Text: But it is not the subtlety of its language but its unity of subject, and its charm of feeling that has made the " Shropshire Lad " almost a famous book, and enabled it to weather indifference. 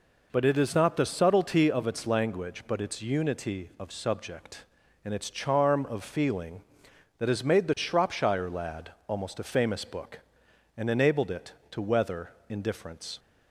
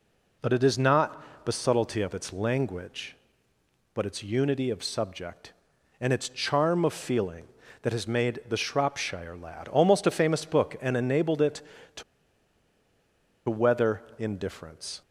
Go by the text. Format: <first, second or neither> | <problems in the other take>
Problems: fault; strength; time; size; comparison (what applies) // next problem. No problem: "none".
first | pauses between "not" and "the"; slight; at 1.2 s; 0.20 s long // pauses between "to" and "weather"; strong; at 12.0 s; 1.4 s long // pauses between "weather" and "indifference"; slight; at 14.0 s; 0.16 s long; slight in the first